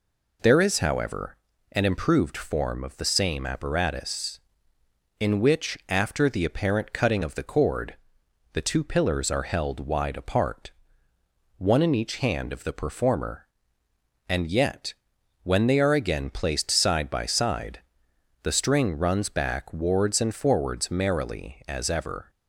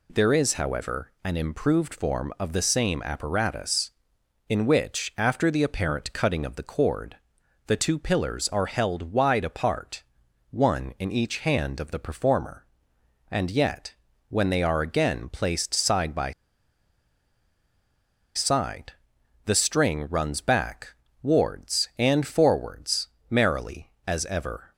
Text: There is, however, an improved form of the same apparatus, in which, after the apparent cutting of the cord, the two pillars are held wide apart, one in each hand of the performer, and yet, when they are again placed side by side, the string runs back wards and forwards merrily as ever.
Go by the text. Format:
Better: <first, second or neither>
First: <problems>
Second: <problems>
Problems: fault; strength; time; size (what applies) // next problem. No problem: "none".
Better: first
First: none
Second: pauses between "by" and "side"; strong; at 16.3 s; 2.0 s long // pauses between "back" and "wards"; slight; at 20.9 s; 0.28 s long // pauses between "forwards" and "merrily"; slight; at 23.0 s; 0.24 s long